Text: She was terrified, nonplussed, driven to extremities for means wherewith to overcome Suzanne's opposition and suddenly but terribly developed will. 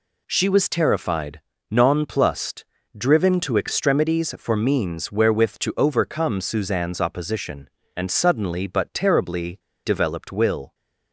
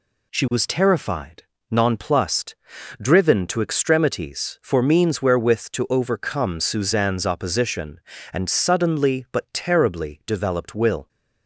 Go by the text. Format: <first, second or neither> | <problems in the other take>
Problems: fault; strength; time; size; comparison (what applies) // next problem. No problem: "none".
second | pauses between "terribly" and "developed"; slight; at 9.5 s; 0.26 s long